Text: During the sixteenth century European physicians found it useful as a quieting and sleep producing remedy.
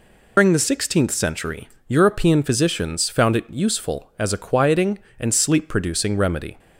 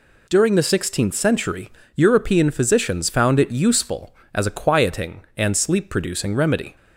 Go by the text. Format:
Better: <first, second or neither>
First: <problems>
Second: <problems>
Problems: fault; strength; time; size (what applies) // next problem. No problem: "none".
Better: second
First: loses the start of "During"; at 0.3 s; 105 ms // pauses between "century" and "European"; slight; at 1.6 s; 0.18 s long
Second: pauses between "century" and "European"; slight; at 1.6 s; 0.26 s long